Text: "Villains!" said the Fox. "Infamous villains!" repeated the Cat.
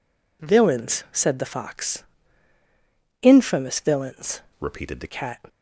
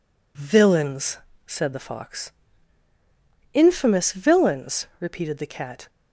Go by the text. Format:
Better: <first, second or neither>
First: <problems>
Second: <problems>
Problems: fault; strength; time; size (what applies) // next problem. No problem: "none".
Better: second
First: changes voice from "repeated" to "the"; from 4.5 to 5.0 s; 0.5 s long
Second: none